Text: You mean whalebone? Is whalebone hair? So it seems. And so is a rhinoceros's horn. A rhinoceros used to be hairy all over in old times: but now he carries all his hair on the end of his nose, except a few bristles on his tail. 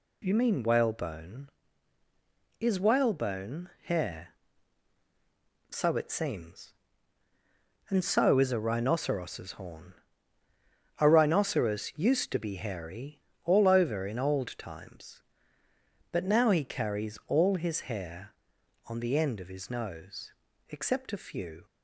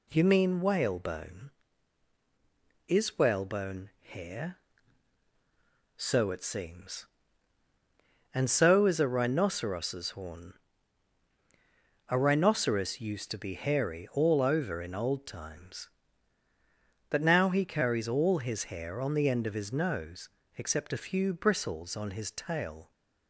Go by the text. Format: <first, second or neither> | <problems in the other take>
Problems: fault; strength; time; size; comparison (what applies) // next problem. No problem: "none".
second | pauses between "whalebone" and "hair"; slight; at 3.6 s; 0.16 s long // pauses between "hairy" and "all"; slight; at 13.1 s; 0.24 s long // stops before "bristles on his tail"; at 21.6 s